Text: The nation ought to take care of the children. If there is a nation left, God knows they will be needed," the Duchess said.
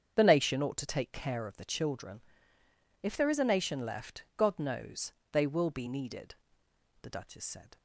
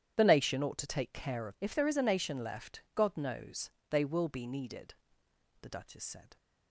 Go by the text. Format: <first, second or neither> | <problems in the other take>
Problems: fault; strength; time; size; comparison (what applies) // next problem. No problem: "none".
first | starts louder than the rest; strong; until 1.2 s; 10 dB; strong in the first // skips "the children"; at 1.5 s // pauses between "knows" and "they"; slight; at 3.7 s; 0.18 s long; slight in the first